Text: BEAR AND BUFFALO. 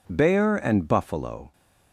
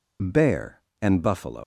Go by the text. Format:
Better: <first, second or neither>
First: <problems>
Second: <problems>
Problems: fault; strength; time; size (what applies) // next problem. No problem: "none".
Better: first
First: none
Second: leaves "BUFFALO" unfinished; at 1.6 s; 155 ms